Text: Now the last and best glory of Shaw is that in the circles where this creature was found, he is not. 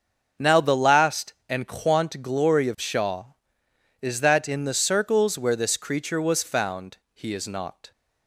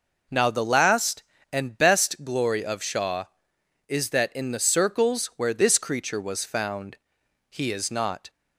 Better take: second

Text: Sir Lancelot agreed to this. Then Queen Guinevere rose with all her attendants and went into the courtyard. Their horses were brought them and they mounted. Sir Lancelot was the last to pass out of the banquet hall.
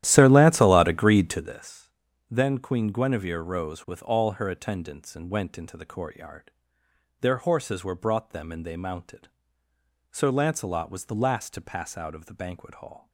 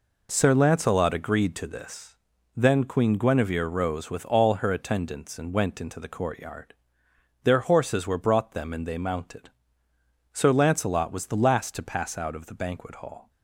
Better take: second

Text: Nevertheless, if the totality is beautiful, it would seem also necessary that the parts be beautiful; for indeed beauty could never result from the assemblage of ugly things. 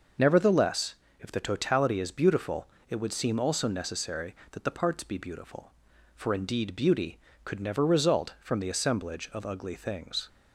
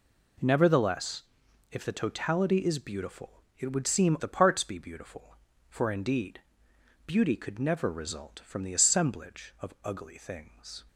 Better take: first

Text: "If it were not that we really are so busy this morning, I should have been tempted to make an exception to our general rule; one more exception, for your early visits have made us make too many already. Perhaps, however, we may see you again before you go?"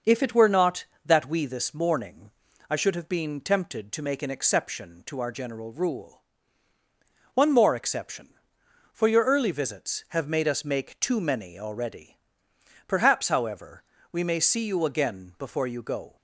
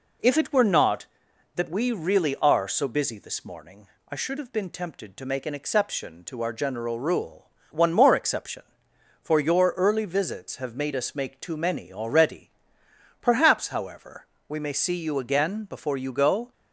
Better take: second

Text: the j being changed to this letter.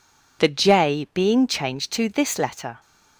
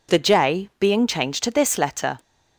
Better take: neither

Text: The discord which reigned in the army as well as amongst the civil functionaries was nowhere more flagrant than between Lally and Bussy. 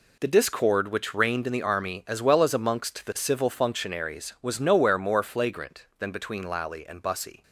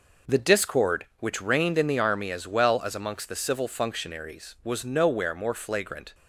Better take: first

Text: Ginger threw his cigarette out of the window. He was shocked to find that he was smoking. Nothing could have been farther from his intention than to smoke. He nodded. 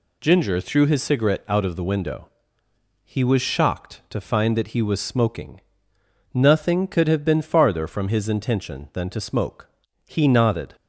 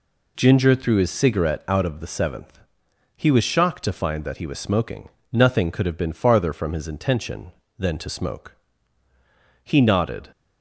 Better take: first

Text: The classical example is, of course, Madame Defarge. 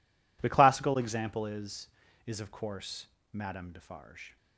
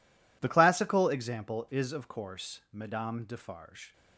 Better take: second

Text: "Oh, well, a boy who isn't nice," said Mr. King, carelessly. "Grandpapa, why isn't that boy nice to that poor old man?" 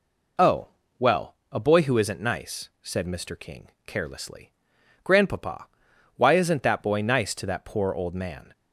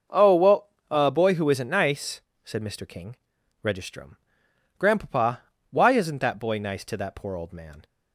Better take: first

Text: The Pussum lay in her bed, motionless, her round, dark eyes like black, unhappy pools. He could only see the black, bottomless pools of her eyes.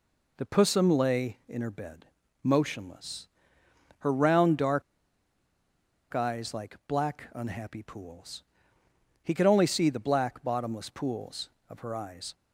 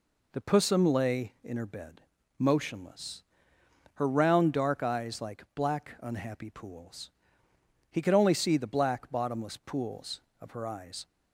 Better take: second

